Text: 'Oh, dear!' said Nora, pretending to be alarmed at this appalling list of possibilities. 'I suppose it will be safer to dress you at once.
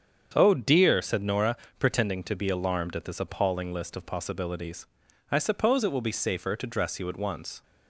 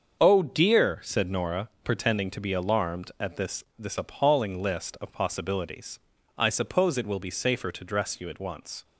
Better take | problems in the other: first | starts louder than the rest; until 1.2 s; 7 dB; strong in the first // says "this" twice; at 3.7 s

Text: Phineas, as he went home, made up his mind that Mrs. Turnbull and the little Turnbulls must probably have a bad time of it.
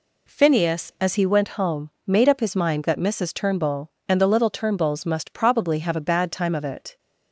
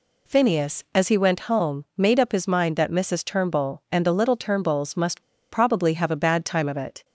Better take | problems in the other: first | pauses between "must" and "probably"; slight; at 5.2 s; 0.28 s long

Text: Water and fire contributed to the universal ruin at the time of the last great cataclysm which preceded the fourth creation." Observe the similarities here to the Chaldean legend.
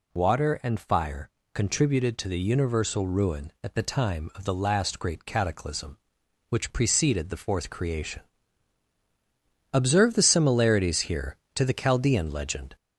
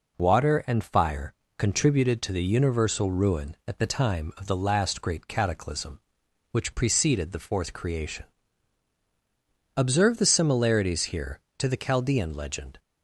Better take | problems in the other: second | gets louder; slight; throughout; 3.5 dB // pauses between "fire" and "contributed"; slight; at 1.3 s; 0.22 s long; slight in the second

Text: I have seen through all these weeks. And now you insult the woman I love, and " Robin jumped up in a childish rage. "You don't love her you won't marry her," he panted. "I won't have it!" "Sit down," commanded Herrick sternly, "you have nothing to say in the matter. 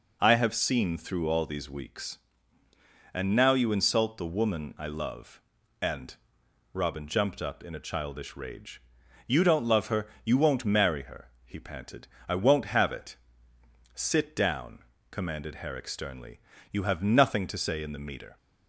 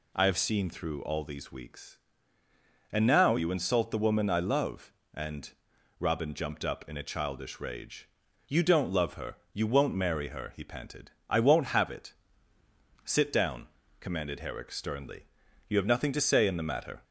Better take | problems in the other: second | pauses between "her" and "you"; slight; at 10.0 s; 0.16 s long; slight in the second // says "meter" for "matter"; at 17.9 s

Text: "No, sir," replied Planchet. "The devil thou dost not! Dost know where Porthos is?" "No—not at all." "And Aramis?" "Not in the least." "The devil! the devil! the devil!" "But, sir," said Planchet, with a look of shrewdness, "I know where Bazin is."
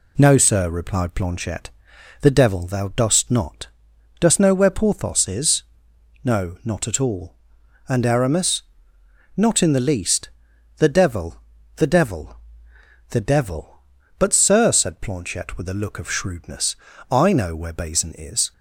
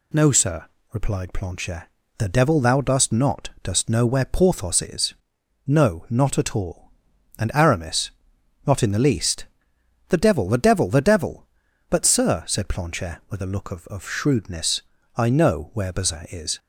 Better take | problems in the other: first | says "of" twice; at 13.8 s

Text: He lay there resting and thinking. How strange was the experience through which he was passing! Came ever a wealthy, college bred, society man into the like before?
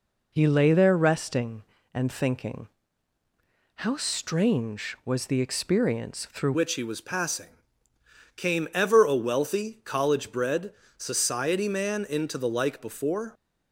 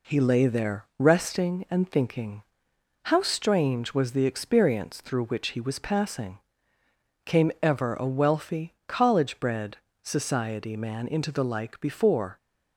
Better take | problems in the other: second | changes voice at "which"; from 6.5 s on; 6.8 s long

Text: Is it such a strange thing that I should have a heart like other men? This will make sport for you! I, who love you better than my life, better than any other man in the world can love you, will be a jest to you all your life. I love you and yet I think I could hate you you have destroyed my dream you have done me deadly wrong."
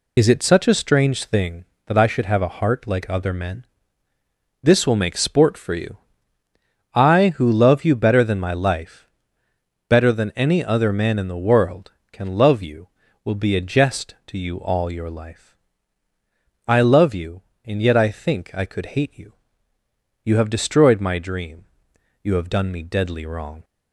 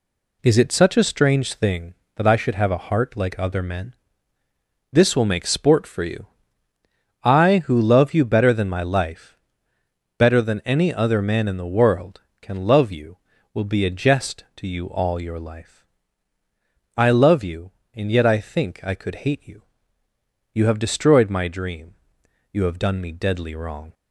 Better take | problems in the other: second | loses the start of "Is"; at 0.1 s; 50 ms // pauses between "you" and "you"; noticeable; at 19.3 s; 0.90 s long; noticeable in the second // pauses between "dream" and "you"; noticeable; at 21.6 s; 0.56 s long; noticeable in the second

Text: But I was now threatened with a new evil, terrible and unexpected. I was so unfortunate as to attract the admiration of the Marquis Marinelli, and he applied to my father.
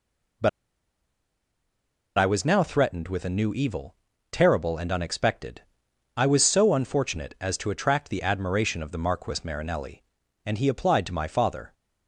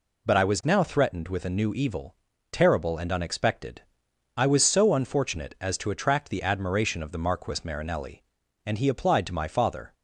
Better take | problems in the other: second | pauses between "But" and "I"; strong; at 0.4 s; 1.6 s long

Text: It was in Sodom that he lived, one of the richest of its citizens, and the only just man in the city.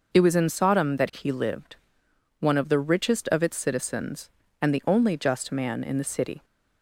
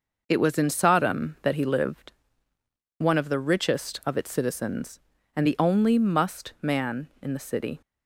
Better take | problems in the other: first | says "must" for "just"; at 5.9 s

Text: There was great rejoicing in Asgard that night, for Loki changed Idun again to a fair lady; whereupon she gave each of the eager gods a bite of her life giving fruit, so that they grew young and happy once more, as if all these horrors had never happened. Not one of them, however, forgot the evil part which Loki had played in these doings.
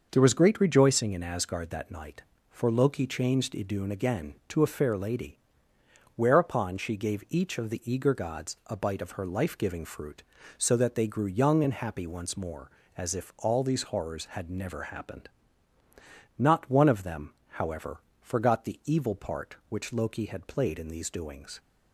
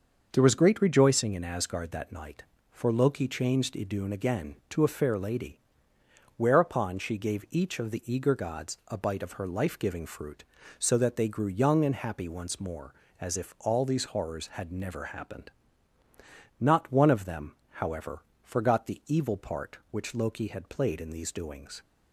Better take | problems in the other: neither | starts louder than the rest; the same in both

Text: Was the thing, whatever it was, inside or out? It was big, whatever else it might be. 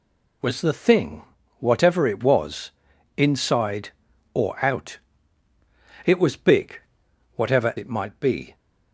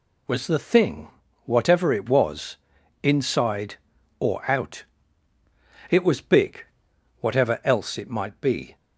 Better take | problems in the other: second | skips "else"; at 7.7 s

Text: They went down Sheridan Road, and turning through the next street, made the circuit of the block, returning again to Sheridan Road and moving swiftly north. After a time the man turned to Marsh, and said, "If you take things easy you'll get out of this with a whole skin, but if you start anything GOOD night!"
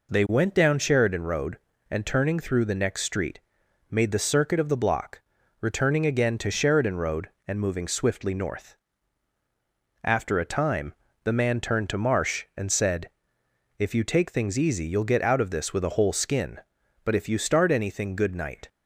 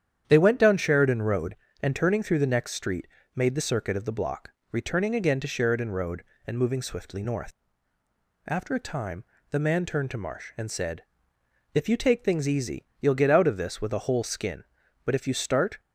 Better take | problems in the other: first | starts louder than the rest; strong; until 1.2 s; 9 dB // pauses between "time" and "the"; slight; at 9.2 s; 0.26 s long; slight in the first // stops before "anything GOOD night"; at 15.7 s

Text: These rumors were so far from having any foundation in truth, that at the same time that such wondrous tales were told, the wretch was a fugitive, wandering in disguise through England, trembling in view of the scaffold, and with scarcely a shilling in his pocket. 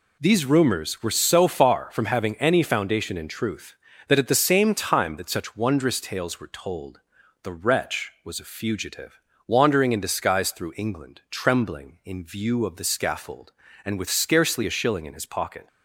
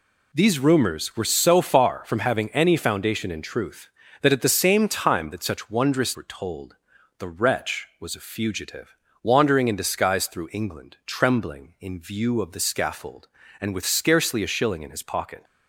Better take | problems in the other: first | skips "tales"; at 6.1 s

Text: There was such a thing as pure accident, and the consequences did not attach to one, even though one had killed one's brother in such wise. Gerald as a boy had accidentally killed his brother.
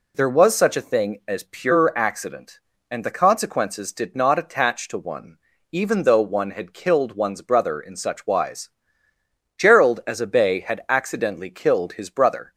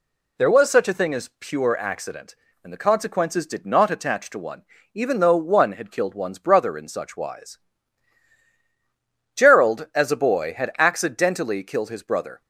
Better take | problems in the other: second | says "bay" for "boy"; at 10.2 s

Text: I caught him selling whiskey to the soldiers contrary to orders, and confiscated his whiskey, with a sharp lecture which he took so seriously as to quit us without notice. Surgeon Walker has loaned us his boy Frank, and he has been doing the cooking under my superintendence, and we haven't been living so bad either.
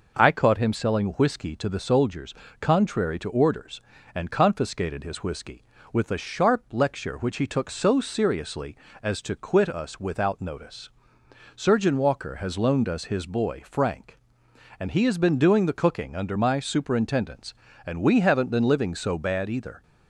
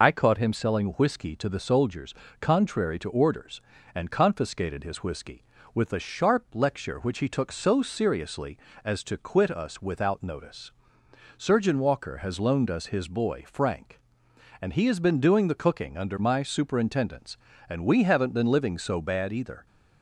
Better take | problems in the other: first | loses the start of "I"; at 0.0 s; 60 ms // pauses between "soldiers" and "contrary"; slight; at 2.1 s; 0.26 s long; slight in the first

